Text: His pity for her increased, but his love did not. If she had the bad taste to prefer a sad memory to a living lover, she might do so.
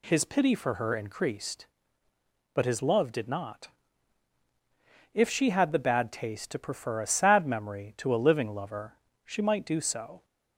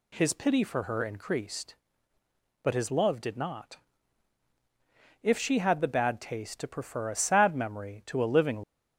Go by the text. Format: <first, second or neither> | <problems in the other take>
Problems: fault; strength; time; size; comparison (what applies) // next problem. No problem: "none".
first | stops before "lover she might do so"; at 8.6 s